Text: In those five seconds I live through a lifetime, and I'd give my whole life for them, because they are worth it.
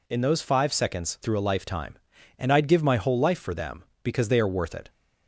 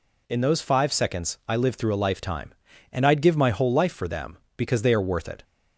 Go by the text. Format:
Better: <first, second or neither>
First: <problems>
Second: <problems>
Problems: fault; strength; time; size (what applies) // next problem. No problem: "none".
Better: second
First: skips "I live"; at 1.1 s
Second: none